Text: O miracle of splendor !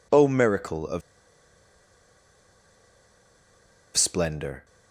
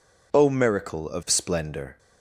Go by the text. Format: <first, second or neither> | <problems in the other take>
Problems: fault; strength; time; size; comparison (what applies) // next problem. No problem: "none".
second | pauses between "of" and "splendor"; strong; at 1.0 s; 2.9 s long